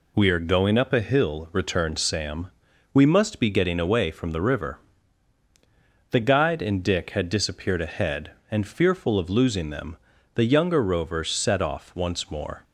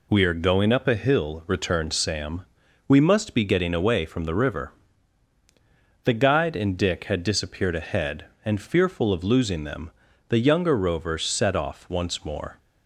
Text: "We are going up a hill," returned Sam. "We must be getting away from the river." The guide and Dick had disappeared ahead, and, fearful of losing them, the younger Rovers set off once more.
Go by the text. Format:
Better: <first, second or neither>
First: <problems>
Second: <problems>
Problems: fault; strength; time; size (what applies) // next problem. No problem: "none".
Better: neither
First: none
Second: none